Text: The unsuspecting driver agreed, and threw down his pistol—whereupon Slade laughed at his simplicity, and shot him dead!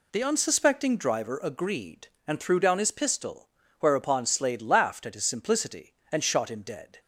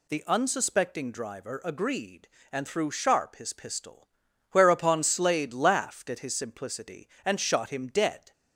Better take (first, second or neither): first